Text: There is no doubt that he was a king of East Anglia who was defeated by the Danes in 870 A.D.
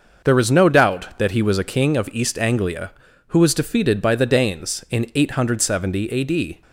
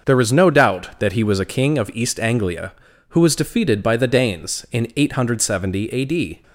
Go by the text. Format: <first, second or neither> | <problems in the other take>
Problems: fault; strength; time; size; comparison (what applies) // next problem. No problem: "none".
neither | starts louder than the rest; noticeable; the same in both